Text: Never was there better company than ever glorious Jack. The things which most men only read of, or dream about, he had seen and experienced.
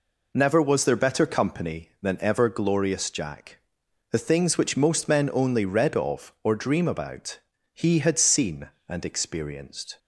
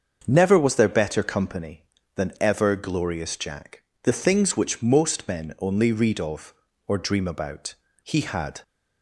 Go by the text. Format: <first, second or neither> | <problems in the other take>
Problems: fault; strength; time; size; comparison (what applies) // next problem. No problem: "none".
first | starts louder than the rest; until 1.2 s; 7 dB // stops before "seen and experienced"; at 8.6 s